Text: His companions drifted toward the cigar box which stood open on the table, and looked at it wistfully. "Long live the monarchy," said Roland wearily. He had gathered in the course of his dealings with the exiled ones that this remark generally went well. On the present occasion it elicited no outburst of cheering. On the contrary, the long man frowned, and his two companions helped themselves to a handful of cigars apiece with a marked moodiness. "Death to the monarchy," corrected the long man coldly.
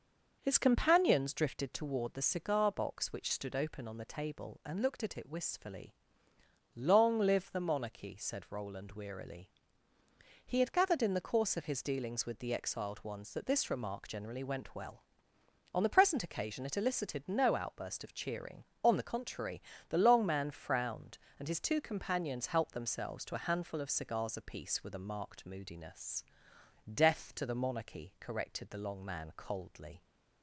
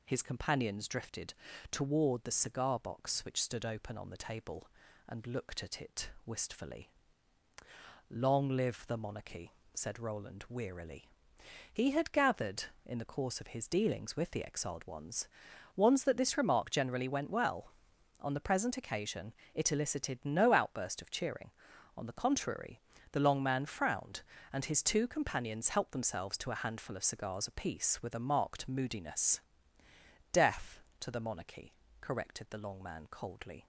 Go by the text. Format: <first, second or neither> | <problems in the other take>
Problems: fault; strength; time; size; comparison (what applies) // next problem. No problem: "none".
first | pauses between "drifted" and "toward"; at 1.3 s; 0.38 s long // pauses between "it" and "wistfully"; slight; at 6.1 s; 0.16 s long // says "ones" twice; at 15.7 s // pauses between "occasion" and "it"; slight; at 19.3 s; 0.20 s long